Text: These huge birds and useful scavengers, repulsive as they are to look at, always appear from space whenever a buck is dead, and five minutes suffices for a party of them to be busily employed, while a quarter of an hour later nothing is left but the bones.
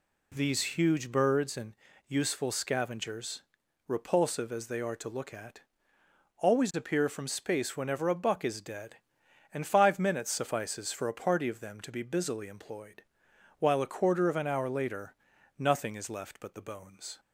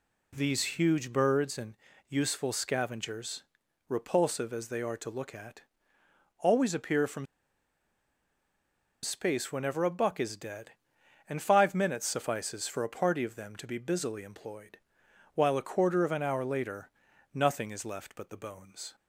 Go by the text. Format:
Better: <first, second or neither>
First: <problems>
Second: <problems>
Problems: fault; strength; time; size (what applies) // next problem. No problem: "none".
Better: first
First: pauses between "and" and "useful"; slight; at 1.7 s; 0.32 s long // pauses between "later" and "nothing"; at 15.1 s; 0.44 s long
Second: pauses between "and" and "useful"; slight; at 1.7 s; 0.32 s long // pauses between "from" and "space"; strong; at 7.2 s; 1.7 s long // pauses between "later" and "nothing"; at 16.8 s; 0.44 s long